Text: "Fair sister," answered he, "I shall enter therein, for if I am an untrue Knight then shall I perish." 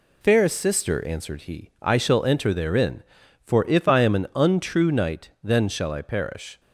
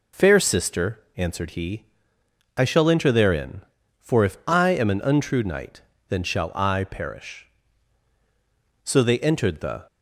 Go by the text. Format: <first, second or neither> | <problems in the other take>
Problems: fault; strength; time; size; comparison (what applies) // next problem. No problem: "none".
first | pauses between "Knight" and "then"; slight; at 5.8 s; 0.28 s long // goes on to say "So they entered the"; noticeable; from 8.8 s on; 1.0 s long